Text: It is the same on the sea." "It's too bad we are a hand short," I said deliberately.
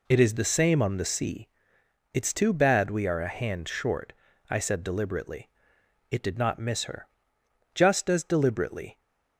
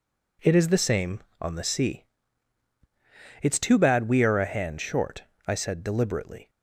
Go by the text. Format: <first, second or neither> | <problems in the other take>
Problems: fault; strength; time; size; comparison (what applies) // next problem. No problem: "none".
second | goes on to say "It did not miss her Just as deliberately"; strong; from 6.1 s on; 2.8 s long